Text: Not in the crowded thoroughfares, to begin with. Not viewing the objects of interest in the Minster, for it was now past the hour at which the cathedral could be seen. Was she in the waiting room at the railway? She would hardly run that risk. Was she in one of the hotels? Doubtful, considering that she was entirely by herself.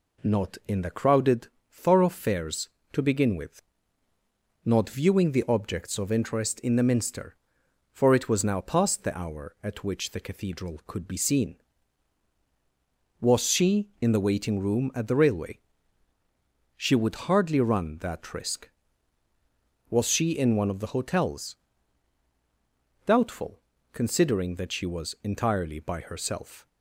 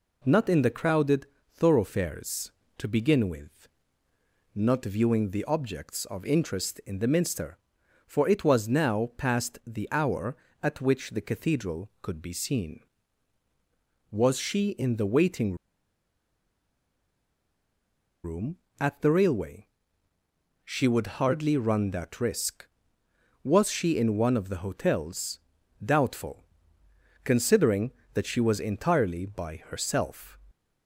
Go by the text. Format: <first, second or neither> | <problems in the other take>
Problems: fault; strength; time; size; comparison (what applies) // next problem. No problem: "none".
first | pauses between "crowded" and "thoroughfares"; slight; at 1.2 s; 0.30 s long; slight in the first // pauses between "waiting" and "room"; strong; at 15.5 s; 2.6 s long